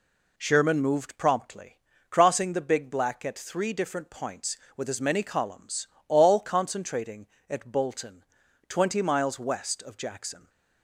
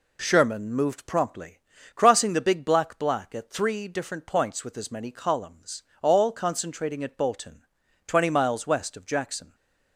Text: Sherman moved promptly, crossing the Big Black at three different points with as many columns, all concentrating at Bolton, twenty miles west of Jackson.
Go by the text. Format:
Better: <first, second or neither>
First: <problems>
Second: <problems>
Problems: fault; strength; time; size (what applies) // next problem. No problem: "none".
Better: first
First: none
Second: says "Black" twice; at 2.9 s // stays silent after the last word; slight; from 9.4 s on; 0.5 s long